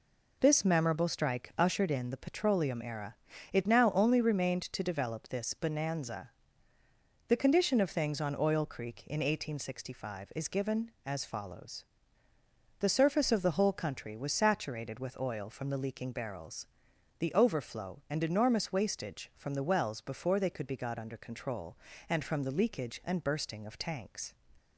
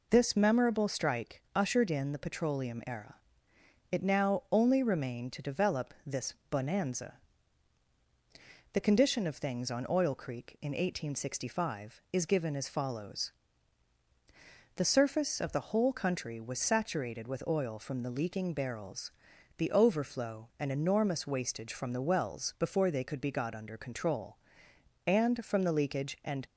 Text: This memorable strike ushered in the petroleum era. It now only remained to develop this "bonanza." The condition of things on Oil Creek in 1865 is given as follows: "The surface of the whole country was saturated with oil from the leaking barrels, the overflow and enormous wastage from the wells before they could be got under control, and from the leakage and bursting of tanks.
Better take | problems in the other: first | pauses between "this" and "bonanza"; slight; at 6.3 s; 0.18 s long // stops before "bursting of tanks"; at 26.4 s

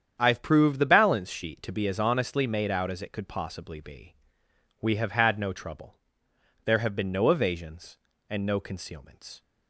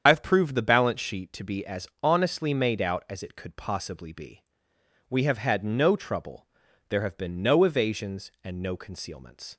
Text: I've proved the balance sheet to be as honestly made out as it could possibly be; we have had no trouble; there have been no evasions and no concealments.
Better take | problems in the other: first | loses the start of "I've"; at 0.0 s; 65 ms // starts louder than the rest; strong; until 1.0 s; 8 dB; strong in the first // pauses between "as" and "honestly"; slight; at 1.8 s; 0.16 s long

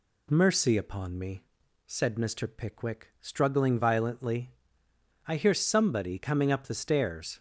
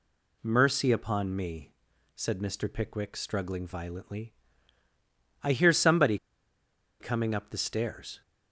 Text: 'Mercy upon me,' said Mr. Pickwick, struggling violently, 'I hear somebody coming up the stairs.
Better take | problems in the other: first | pauses between "somebody" and "coming"; noticeable; at 6.1 s; 0.84 s long

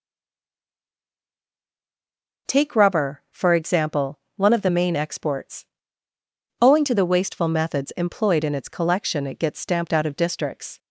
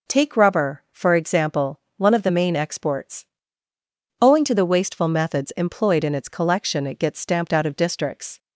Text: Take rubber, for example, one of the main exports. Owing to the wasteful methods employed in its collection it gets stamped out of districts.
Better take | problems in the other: second | stays silent before the first word; until 2.4 s; 2.4 s long

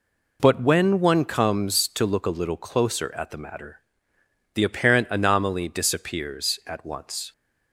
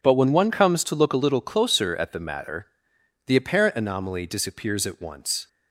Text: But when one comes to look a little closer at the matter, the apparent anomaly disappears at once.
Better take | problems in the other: neither | none

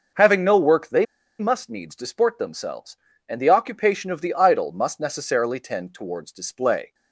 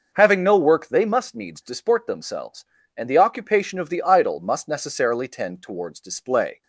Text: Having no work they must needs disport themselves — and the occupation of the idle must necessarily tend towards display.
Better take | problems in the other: second | pauses between "they" and "must"; slight; at 1.0 s; 0.34 s long

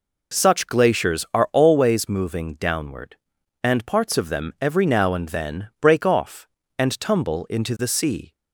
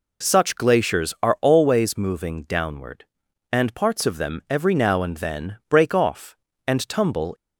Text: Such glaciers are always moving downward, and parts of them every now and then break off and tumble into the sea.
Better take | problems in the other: first | stops before "into the sea"; at 7.3 s

